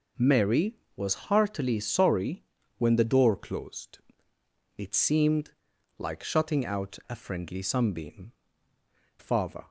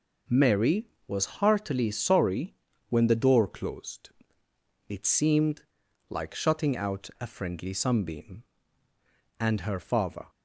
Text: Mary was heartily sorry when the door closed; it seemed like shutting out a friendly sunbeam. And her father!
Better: second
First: pauses between "sorry" and "when"; slight; at 2.4 s; 0.34 s long // pauses between "seemed" and "like"; noticeable; at 5.4 s; 0.48 s long // skips "And her"; at 8.7 s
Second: pauses between "sorry" and "when"; slight; at 2.5 s; 0.34 s long // pauses between "seemed" and "like"; noticeable; at 5.6 s; 0.48 s long

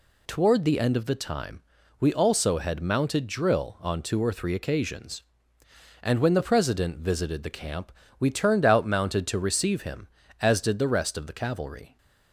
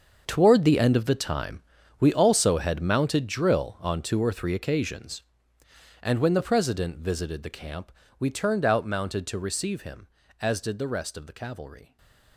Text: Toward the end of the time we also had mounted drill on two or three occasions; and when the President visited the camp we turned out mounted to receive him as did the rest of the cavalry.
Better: first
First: pauses between "time" and "we"; at 1.6 s; 0.38 s long // pauses between "camp" and "we"; slight; at 7.9 s; 0.26 s long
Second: gets quieter; strong; throughout; 15 dB // pauses between "time" and "we"; at 1.6 s; 0.38 s long // pauses between "camp" and "we"; slight; at 7.9 s; 0.26 s long // stays silent after the last word; slight; from 11.8 s on; 0.5 s long

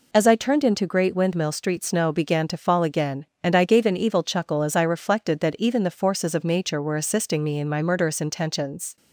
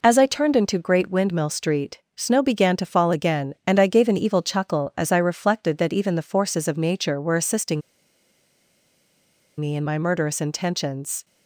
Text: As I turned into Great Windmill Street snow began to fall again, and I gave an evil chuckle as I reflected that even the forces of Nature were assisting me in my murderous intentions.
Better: first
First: none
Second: pauses between "Street" and "snow"; slight; at 1.9 s; 0.20 s long // pauses between "assisting" and "me"; strong; at 7.8 s; 1.7 s long

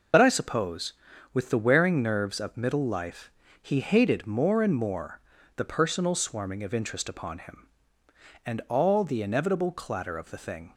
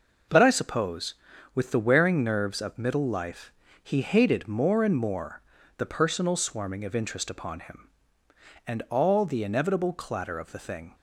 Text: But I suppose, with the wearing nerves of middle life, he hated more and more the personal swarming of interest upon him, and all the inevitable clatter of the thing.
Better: second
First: loses the start of "But"; at 0.1 s; 65 ms // pauses between "more" and "the"; slight; at 5.1 s; 0.36 s long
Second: pauses between "more" and "the"; slight; at 5.4 s; 0.36 s long

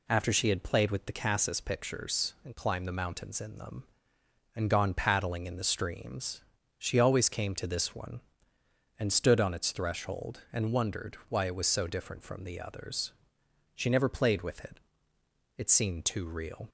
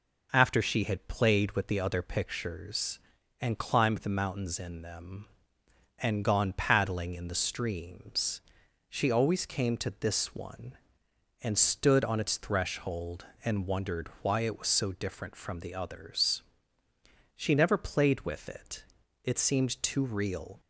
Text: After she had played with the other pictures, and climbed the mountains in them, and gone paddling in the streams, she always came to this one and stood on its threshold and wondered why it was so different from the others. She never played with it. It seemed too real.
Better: second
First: says "cassis" for "other"; at 1.1 s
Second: none

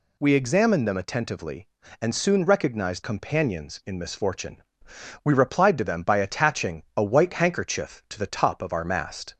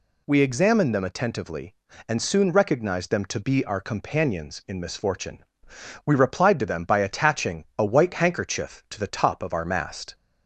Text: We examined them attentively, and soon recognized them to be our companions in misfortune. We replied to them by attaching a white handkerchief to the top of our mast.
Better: second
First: skips "them to be our"; at 3.0 s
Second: none

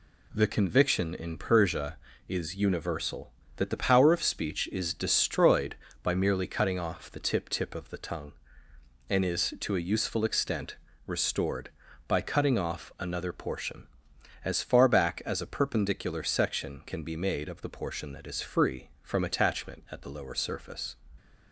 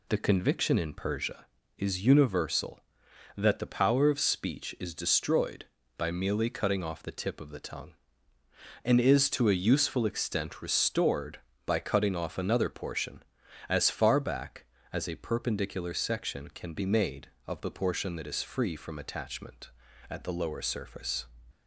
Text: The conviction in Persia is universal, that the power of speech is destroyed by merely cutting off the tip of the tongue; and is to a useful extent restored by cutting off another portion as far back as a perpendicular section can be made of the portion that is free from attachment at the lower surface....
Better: second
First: says "tip" twice; at 7.4 s // pauses between "extent" and "restored"; slight; at 10.7 s; 0.32 s long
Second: none

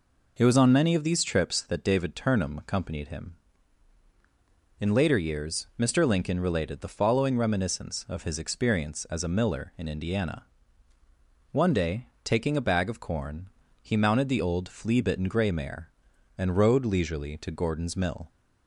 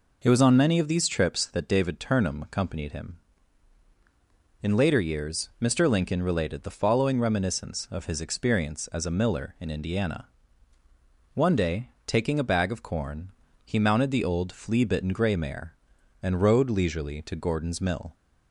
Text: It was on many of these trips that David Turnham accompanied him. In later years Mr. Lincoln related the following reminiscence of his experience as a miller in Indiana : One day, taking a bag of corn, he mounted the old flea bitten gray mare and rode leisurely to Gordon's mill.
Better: neither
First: none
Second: none

